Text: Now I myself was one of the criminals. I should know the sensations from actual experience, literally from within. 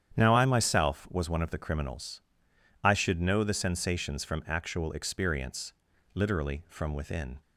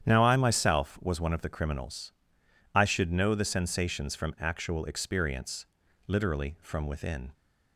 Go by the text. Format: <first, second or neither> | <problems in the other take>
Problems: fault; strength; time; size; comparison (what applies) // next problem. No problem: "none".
neither | starts louder than the rest; strong; the same in both